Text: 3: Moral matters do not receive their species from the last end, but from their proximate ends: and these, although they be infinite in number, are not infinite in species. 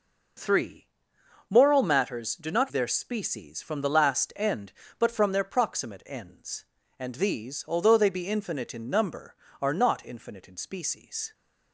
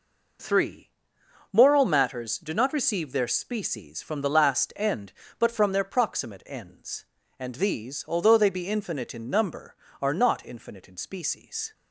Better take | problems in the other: second | skips "receive"; at 2.7 s

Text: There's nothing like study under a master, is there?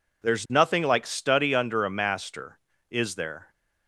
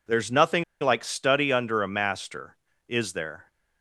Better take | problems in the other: first | pauses between "nothing" and "like"; slight; at 0.6 s; 0.17 s long

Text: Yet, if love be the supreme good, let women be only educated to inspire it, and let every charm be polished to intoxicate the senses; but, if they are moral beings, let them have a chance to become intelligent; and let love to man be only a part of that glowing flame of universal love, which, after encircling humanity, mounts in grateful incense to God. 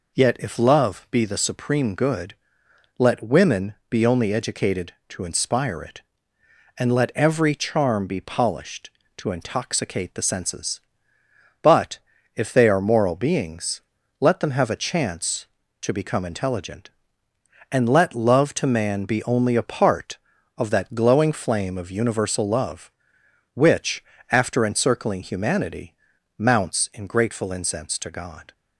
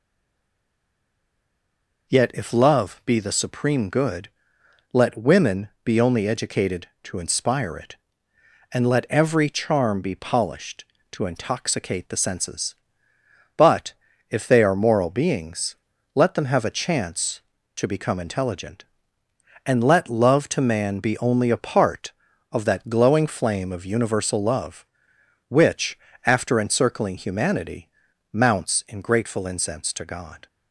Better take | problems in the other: first | stays silent before the first word; noticeable; until 2.0 s; 2.0 s long // pauses between "women" and "be"; slight; at 5.6 s; 0.16 s long; slight in the first

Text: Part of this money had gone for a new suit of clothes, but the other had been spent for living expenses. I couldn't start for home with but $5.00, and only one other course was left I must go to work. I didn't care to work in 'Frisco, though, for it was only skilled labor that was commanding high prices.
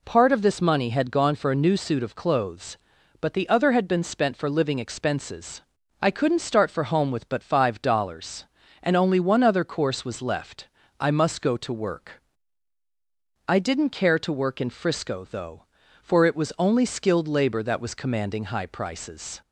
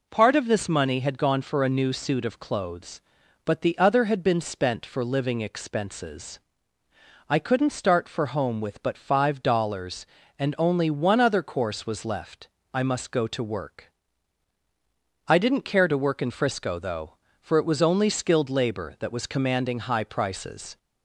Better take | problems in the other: neither | pauses between "left" and "I"; slight; the same in both

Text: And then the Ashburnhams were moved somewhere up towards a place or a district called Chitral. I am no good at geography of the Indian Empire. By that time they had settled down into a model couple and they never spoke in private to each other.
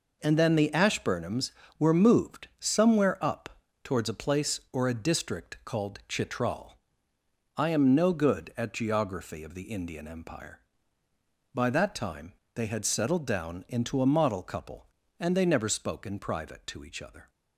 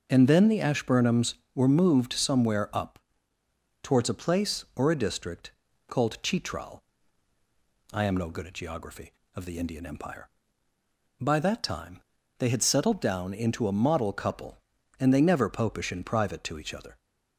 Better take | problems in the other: first | pauses between "up" and "towards"; noticeable; at 2.9 s; 0.82 s long; slight in the first // pauses between "district" and "called"; at 5.5 s; 0.38 s long // pauses between "time" and "they"; at 12.0 s; 0.38 s long; slight in the first // says "popish" for "spoke"; at 15.4 s

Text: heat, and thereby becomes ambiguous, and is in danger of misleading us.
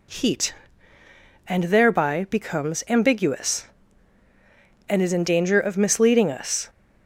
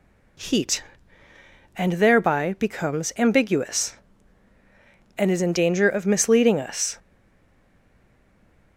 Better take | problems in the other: first | stays silent after the last word; noticeable; from 6.9 s on; 1.8 s long

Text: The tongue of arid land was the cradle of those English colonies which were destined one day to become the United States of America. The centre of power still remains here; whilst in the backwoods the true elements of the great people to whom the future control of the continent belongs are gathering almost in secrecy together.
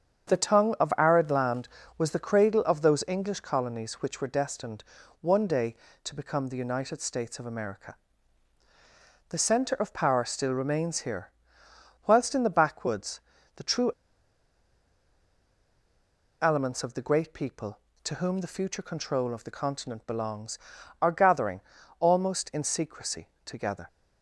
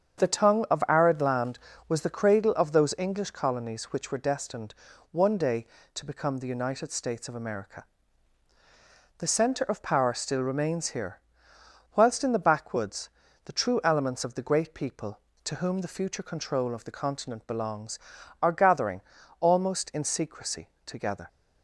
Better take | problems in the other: second | starts louder than the rest; strong; until 1.3 s; 7.5 dB; strong in the second // pauses between "destined" and "one"; at 4.8 s; 0.38 s long; also in the second // pauses between "backwoods" and "the"; slight; at 13.2 s; 0.34 s long; slight in the second // pauses between "true" and "elements"; strong; at 13.9 s; 2.5 s long // pauses between "gathering" and "almost"; at 21.6 s; 0.38 s long; also in the second // pauses between "secrecy" and "together"; slight; at 23.2 s; 0.16 s long; slight in the second

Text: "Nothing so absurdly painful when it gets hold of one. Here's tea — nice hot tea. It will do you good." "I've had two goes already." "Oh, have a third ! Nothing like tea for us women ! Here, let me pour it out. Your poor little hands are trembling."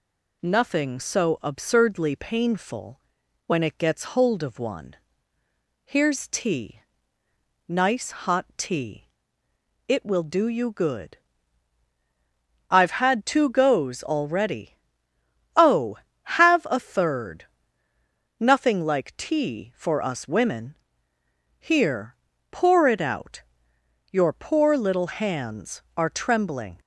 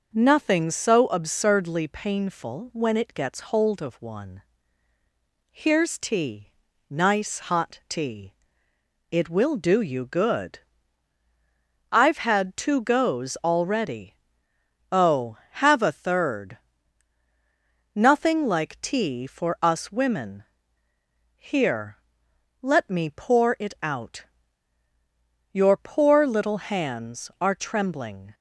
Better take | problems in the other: second | pauses between "painful" and "when"; noticeable; at 2.9 s; 0.48 s long // skips "let me"; at 22.3 s

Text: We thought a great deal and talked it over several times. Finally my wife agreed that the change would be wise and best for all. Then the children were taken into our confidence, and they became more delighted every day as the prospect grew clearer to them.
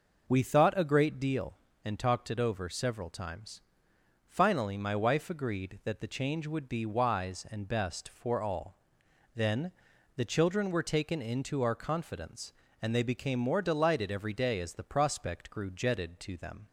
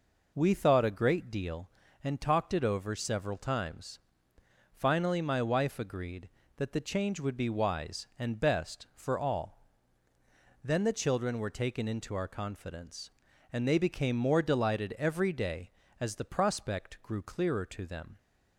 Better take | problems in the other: second | pauses between "Then" and "the"; noticeable; at 9.7 s; 0.46 s long // says "jetted" for "clearer"; at 15.7 s

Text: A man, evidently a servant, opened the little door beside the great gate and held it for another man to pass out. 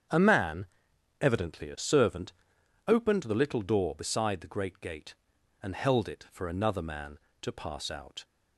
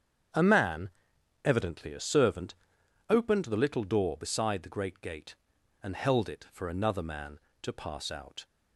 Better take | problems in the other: neither | starts louder than the rest; strong; the same in both

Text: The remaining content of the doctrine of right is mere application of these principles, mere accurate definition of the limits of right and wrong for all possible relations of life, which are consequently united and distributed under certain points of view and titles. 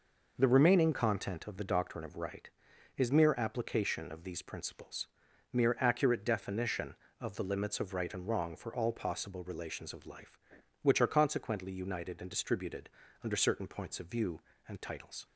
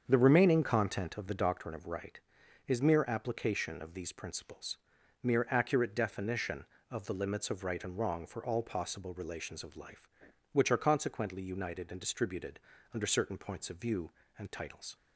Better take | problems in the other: first | starts louder than the rest; strong; until 1.6 s; 7.5 dB // pauses between "distributed" and "under"; slight; at 12.5 s; 0.34 s long; slight in the first

